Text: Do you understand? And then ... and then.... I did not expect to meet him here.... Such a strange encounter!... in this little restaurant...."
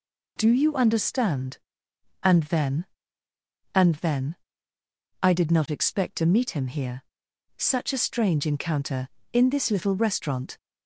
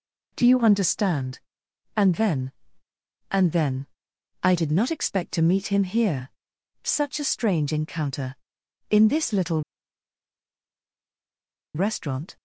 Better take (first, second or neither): first